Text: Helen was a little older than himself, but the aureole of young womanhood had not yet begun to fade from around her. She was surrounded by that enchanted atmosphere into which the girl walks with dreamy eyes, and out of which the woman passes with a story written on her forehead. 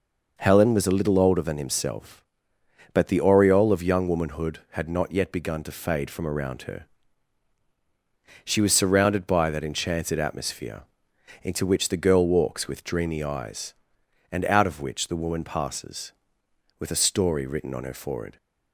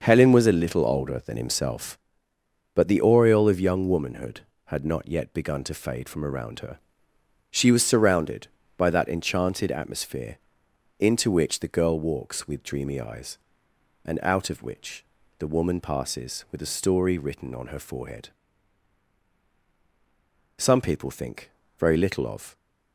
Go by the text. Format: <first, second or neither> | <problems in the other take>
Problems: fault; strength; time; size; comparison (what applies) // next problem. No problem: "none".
first | starts louder than the rest; until 1.0 s; 6 dB // pauses between "atmosphere" and "into"; noticeable; at 10.3 s; 0.60 s long; noticeable in the first // pauses between "which" and "the"; slight; at 15.0 s; 0.34 s long // goes on to say "Some people think very little of"; strong; from 20.5 s on; 1.9 s long